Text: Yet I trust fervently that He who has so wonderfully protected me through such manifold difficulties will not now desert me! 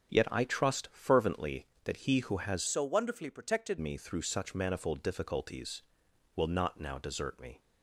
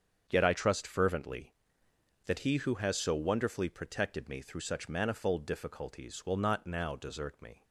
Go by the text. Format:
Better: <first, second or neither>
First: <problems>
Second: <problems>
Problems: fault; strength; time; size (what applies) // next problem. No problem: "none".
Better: second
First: starts louder than the rest; strong; until 1.2 s; 8 dB // changes voice from "so" to "protected"; from 2.6 to 3.7 s; 1.1 s long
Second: starts louder than the rest; strong; until 1.2 s; 7.5 dB